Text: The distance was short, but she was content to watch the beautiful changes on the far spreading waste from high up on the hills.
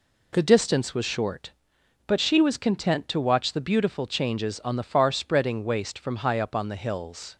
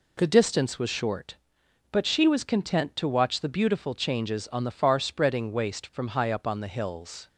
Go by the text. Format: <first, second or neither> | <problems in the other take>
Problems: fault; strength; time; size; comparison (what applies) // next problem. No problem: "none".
neither | none